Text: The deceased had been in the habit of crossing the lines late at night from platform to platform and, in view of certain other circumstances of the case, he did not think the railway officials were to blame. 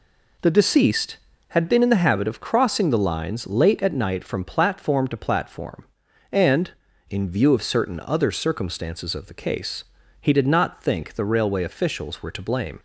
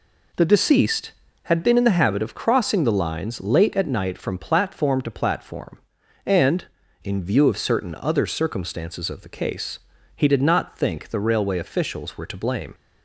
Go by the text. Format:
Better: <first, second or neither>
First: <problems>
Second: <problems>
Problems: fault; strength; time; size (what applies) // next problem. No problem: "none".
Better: neither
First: none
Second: none